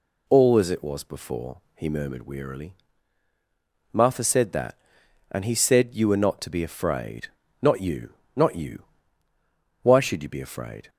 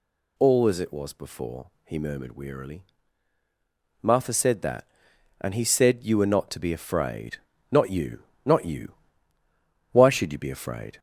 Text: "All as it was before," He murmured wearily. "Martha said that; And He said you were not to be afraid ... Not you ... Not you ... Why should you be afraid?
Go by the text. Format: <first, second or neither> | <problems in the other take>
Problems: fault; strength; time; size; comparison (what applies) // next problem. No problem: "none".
first | gets louder; slight; throughout; 3 dB